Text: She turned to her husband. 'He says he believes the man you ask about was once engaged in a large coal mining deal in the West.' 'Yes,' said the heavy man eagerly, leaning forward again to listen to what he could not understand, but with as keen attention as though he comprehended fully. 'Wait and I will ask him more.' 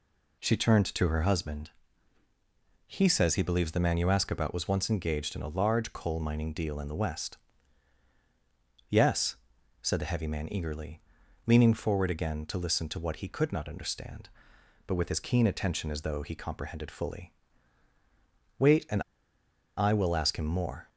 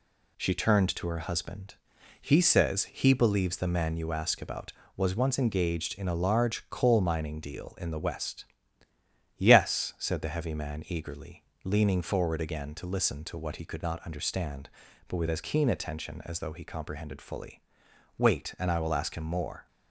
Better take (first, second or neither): second